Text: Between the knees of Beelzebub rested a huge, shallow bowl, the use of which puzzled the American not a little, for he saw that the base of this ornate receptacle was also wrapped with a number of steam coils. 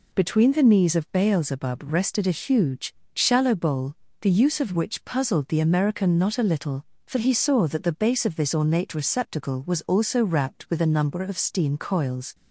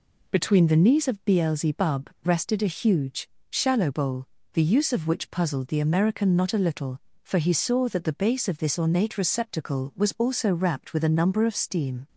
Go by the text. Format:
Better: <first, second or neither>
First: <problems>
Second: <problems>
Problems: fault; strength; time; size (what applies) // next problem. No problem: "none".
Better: first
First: none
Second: pauses between "Beelzebub" and "rested"; slight; at 2.0 s; 0.16 s long // stops before "coils"; at 12.0 s